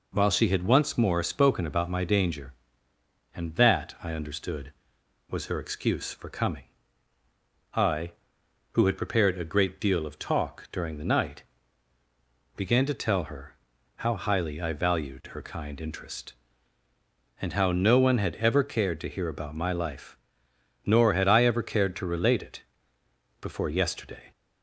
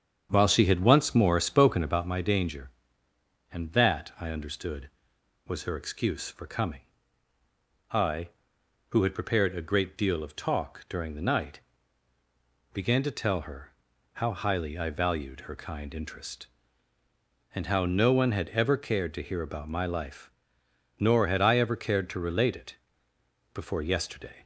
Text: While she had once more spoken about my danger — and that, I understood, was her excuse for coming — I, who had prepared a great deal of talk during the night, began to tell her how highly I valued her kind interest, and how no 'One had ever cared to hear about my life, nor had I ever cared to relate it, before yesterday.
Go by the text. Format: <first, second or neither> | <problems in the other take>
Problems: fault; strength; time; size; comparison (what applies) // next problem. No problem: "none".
first | starts louder than the rest; strong; until 2.1 s; 7.5 dB // pauses between "her" and "how"; at 13.7 s; 0.40 s long; also in the first